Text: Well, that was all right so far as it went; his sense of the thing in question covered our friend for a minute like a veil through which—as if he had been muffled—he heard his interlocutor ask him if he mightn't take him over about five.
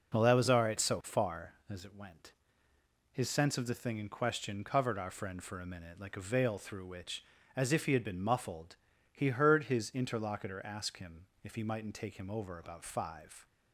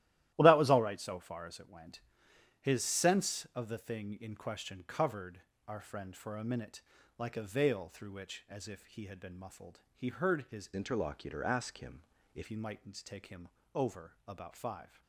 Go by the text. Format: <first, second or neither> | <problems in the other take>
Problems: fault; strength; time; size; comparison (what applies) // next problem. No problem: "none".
first | starts louder than the rest; strong; until 1.3 s; 14 dB // pauses between "covered" and "our"; slight; at 5.4 s; 0.26 s long // pauses between "minute" and "like"; at 6.8 s; 0.38 s long // changes voice from "interlocutor" to "if"; from 10.7 to 12.4 s; 1.7 s long // pauses between "him" and "if"; slight; at 12.0 s; 0.32 s long; slight in the first // pauses between "him" and "over"; slight; at 13.4 s; 0.26 s long // pauses between "over" and "about"; slight; at 14.1 s; 0.16 s long